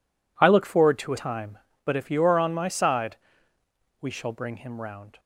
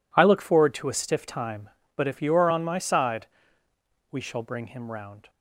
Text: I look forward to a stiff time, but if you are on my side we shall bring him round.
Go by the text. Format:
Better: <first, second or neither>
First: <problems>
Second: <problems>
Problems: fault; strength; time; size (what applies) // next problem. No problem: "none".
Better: second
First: skips "stiff"; at 1.1 s // pauses between "side" and "we"; noticeable; at 3.1 s; 0.84 s long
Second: pauses between "side" and "we"; noticeable; at 3.2 s; 0.84 s long